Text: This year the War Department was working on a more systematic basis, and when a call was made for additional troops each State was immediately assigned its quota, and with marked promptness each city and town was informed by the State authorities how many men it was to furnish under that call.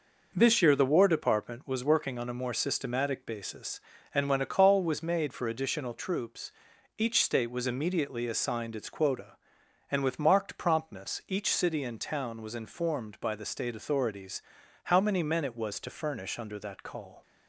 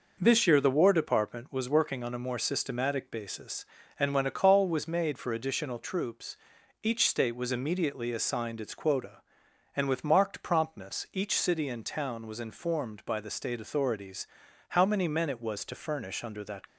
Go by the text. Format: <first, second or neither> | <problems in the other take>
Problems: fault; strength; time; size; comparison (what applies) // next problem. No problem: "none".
first | pauses between "troops" and "each"; noticeable; at 6.3 s; 0.46 s long; noticeable in the first // pauses between "authorities" and "how"; at 14.2 s; 0.42 s long; also in the first // stops before "call"; at 16.6 s